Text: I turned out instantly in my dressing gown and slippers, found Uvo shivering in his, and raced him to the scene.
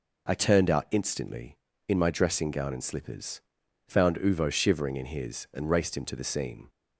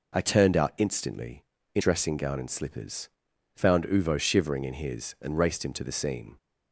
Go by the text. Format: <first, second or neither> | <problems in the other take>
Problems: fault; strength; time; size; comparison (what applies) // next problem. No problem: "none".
first | skips "my"; at 1.8 s